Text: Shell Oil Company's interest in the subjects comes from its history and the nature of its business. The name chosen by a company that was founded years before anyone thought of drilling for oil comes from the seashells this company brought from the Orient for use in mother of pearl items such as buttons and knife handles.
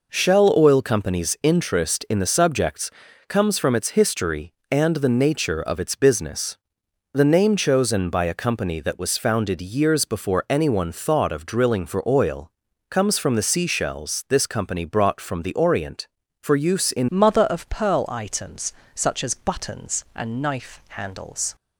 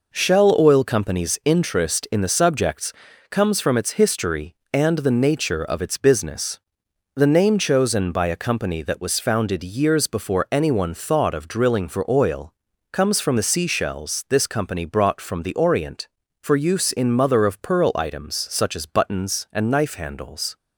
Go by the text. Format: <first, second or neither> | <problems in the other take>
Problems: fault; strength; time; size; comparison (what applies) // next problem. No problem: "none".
second | pauses between "subjects" and "comes"; at 2.8 s; 0.38 s long; also in the second // pauses between "oil" and "comes"; at 12.4 s; 0.40 s long; also in the second // changes voice at "mother"; from 17.0 s on; 4.5 s long // pauses between "items" and "such"; slight; at 18.7 s; 0.24 s long